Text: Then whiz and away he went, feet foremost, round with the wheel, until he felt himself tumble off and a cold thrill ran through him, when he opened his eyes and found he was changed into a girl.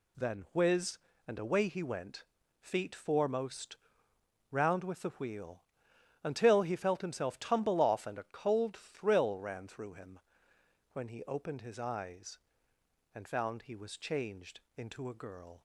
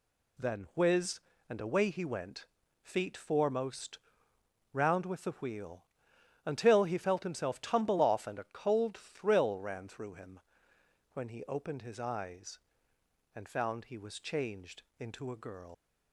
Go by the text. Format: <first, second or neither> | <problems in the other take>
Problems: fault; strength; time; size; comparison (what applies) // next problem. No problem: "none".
first | pauses between "changed" and "into"; slight; at 14.8 s; 0.16 s long; slight in the first // leaves "girl" unfinished; at 15.7 s; 85 ms